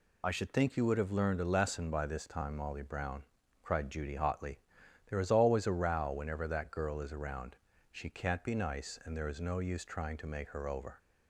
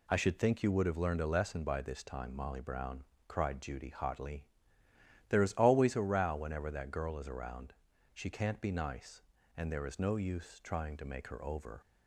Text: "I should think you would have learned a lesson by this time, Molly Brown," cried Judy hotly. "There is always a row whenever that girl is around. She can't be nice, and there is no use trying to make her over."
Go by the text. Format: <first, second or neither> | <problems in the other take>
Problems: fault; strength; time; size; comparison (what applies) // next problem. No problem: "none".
second | loses the start of "I"; at 0.2 s; 50 ms